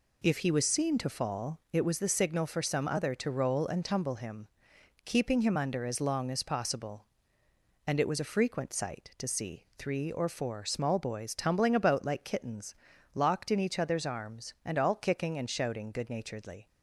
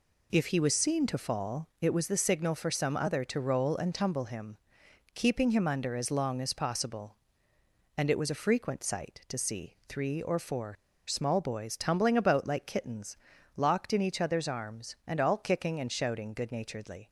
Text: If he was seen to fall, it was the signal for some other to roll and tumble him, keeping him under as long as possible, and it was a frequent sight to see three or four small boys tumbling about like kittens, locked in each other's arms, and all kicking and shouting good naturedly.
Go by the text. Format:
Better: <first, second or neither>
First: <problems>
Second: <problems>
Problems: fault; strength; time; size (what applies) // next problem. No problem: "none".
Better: first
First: none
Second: pauses between "four" and "small"; slight; at 10.7 s; 0.33 s long